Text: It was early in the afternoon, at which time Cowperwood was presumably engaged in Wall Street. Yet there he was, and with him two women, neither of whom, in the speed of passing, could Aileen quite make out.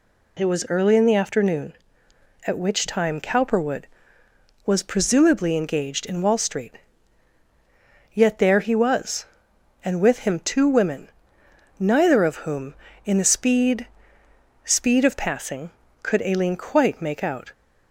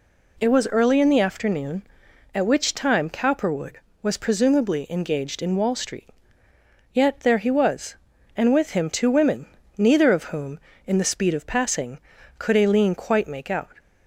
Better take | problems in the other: second | says "speed" twice; at 14.6 s

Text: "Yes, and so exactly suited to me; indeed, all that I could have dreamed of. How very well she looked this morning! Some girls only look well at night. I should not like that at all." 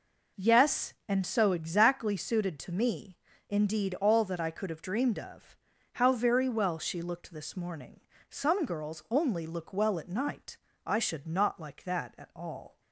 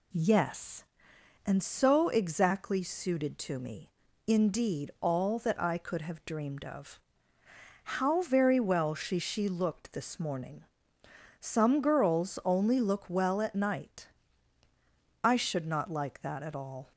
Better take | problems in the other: first | says "she" twice; at 9.1 s

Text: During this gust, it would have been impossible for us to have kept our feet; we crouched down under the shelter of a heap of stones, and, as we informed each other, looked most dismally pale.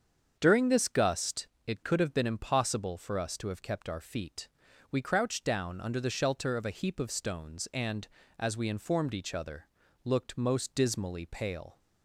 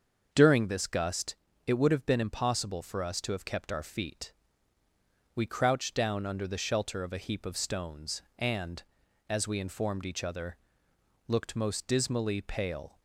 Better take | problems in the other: second | starts louder than the rest; strong; until 1.4 s; 7 dB; also in the second // says "could" for "would"; at 1.8 s

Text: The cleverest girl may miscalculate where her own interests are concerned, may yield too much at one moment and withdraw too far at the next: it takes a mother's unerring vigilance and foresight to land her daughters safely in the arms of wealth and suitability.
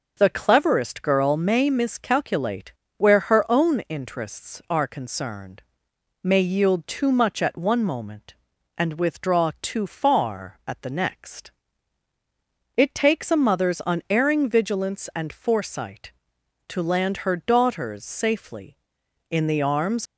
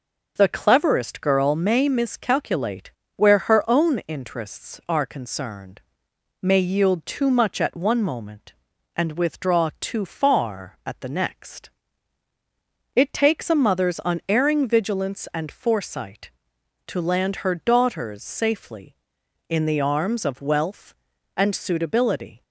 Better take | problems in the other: second | pauses between "miscalculate" and "where"; slight; at 2.7 s; 0.24 s long; slight in the second // stops before "of wealth and suitability"; at 20.0 s

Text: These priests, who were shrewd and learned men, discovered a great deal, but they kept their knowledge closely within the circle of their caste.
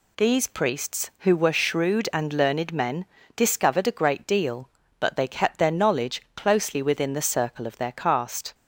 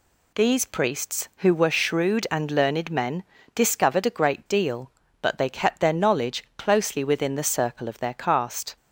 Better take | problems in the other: neither | none

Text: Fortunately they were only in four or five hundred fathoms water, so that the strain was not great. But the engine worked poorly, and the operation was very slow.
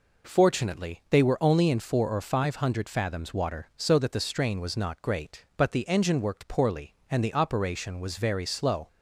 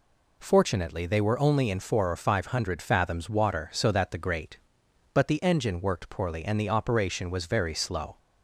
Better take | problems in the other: first | skips "strain was not"; at 4.1 s

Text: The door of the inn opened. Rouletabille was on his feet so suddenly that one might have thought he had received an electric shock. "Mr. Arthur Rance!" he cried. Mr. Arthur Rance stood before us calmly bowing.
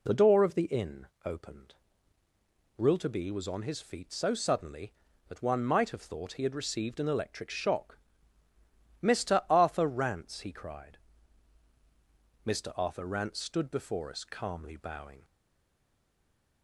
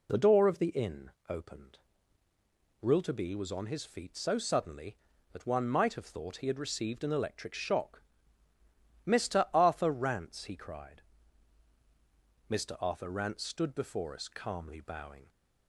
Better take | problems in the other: second | pauses between "inn" and "opened"; slight; at 1.0 s; 0.18 s long; slight in the second // stays silent after the last word; noticeable; from 15.2 s on; 1.4 s long

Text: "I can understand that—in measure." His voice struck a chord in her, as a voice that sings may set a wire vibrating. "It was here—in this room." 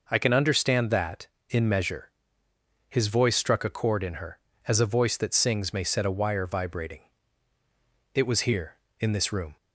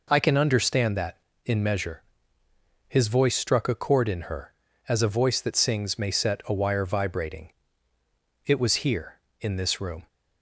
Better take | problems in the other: neither | none

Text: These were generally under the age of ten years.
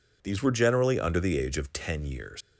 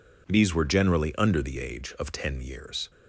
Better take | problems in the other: second | leaves "years" unfinished; at 2.4 s; 80 ms

